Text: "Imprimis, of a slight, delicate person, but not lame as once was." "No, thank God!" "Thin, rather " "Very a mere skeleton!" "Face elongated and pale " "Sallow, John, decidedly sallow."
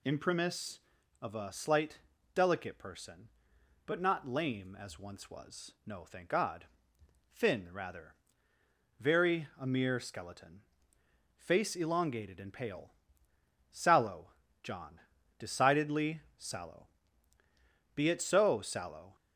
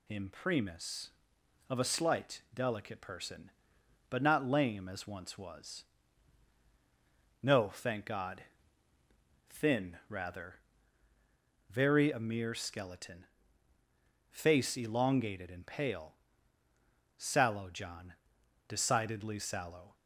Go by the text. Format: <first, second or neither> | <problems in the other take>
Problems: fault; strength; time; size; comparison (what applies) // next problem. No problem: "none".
second | pauses between "decidedly" and "sallow"; slight; at 16.2 s; 0.16 s long // goes on to say "Be it so sallow"; noticeable; from 17.9 s on; 1.2 s long